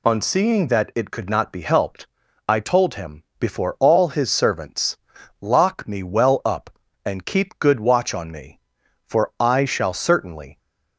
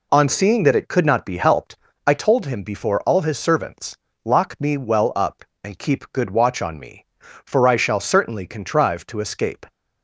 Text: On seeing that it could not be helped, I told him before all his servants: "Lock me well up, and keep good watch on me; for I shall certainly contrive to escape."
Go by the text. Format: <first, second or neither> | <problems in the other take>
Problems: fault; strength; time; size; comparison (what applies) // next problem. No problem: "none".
second | pauses between "him" and "before"; slight; at 3.2 s; 0.16 s long // stops before "contrive to escape"; at 10.5 s